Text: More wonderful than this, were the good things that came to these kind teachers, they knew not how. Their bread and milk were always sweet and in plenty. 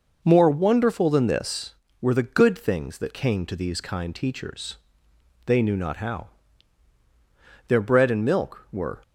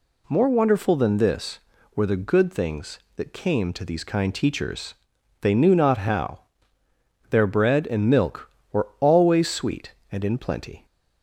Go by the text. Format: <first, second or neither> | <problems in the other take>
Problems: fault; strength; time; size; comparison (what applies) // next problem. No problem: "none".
second | stops before "always sweet and in plenty"; at 9.0 s